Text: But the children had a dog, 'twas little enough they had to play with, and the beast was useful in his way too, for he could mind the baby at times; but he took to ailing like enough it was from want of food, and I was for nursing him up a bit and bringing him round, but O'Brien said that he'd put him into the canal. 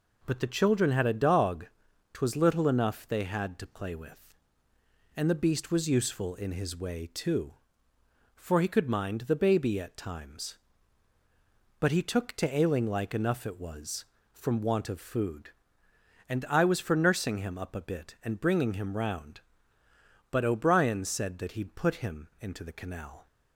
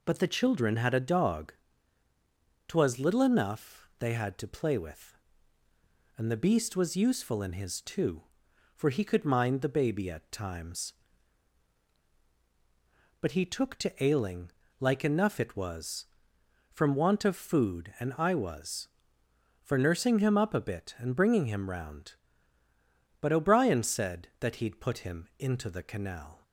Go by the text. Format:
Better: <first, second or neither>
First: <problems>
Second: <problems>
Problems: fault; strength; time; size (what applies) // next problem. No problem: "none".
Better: first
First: none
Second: skips "way"; at 7.7 s // pauses between "ailing" and "like"; slight; at 14.5 s; 0.30 s long